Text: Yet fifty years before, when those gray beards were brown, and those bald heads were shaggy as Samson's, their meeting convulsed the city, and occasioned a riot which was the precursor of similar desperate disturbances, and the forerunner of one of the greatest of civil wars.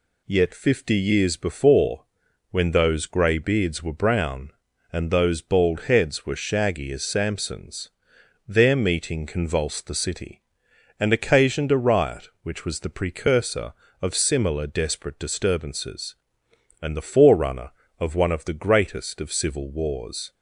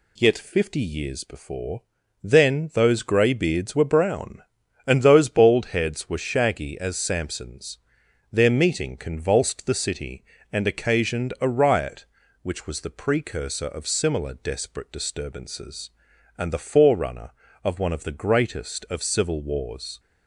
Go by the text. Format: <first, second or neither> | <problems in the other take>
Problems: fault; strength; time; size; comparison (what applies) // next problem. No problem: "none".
first | says "then" for "when"; at 2.2 s